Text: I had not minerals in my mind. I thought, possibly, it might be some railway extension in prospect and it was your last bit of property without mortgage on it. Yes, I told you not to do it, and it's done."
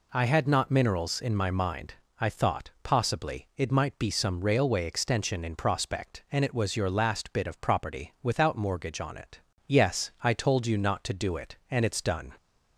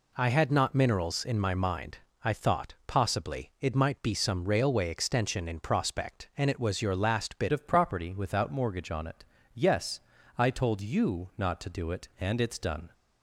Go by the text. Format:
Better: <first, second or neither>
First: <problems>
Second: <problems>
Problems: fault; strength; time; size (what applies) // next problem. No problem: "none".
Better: first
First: none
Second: changes voice at "of"; from 7.5 s on; 5.4 s long